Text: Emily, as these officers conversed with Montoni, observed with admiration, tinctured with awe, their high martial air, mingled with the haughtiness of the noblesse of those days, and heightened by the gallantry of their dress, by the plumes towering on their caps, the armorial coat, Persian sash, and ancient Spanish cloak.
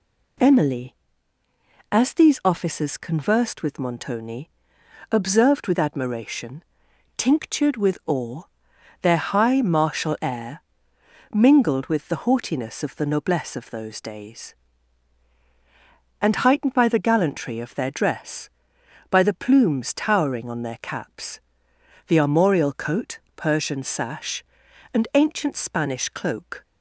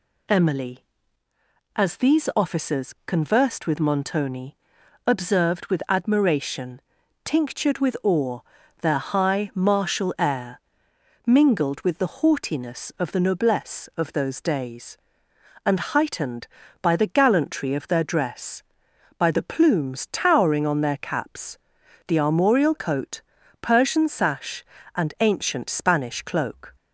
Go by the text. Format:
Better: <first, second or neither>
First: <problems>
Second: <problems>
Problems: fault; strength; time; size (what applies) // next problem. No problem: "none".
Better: neither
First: none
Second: none